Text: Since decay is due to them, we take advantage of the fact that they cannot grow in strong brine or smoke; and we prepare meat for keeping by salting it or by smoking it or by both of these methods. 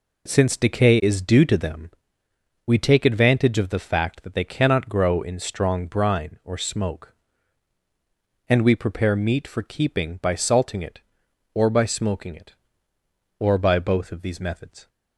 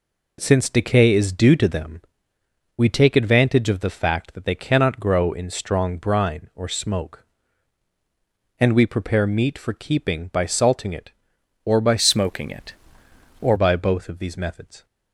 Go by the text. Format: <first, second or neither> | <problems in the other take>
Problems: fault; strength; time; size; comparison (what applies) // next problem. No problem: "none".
first | changes voice from "smoking" to "or"; from 11.9 to 13.5 s; 1.6 s long